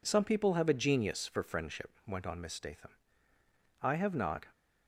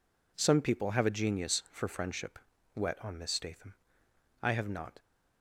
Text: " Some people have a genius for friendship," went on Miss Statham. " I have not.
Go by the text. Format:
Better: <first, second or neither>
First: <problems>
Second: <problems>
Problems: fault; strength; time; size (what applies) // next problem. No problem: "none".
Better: first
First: none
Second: says "wet" for "went"; at 2.7 s